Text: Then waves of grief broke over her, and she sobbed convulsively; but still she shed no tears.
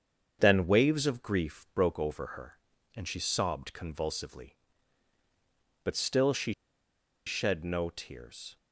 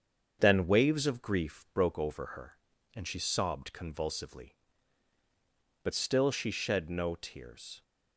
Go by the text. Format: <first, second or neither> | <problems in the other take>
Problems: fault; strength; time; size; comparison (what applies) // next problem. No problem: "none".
second | starts louder than the rest; strong; until 1.4 s; 7.5 dB; strong in the second // pauses between "she" and "shed"; noticeable; at 6.5 s; 0.72 s long